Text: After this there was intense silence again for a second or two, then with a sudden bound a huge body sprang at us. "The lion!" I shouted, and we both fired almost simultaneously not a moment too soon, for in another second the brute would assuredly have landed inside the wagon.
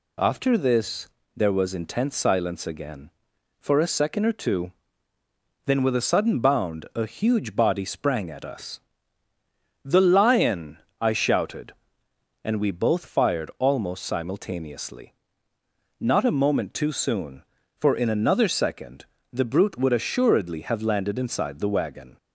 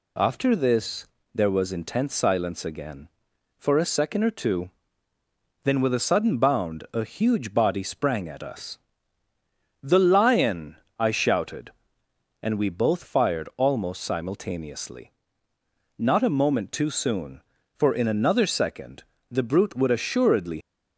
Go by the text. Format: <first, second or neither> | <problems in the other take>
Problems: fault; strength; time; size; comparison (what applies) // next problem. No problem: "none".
first | pauses between "this" and "there"; slight; at 1.0 s; 0.30 s long; slight in the first // pauses between "simultaneously" and "not"; noticeable; at 15.1 s; 0.88 s long; noticeable in the first // pauses between "second" and "the"; slight; at 19.0 s; 0.26 s long; slight in the first // stops before "have landed inside the wagon"; at 20.6 s